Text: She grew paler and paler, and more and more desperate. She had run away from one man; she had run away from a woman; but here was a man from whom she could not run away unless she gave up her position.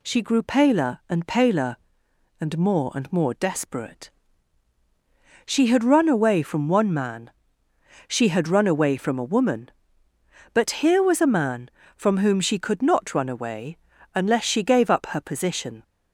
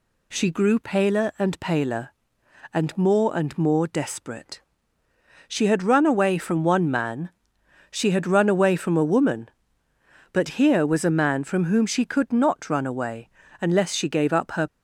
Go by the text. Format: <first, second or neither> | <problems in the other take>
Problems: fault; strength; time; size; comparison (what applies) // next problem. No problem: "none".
first | pauses between "away" and "unless"; slight; at 13.2 s; 0.32 s long; also in the first // stops before "position"; at 14.6 s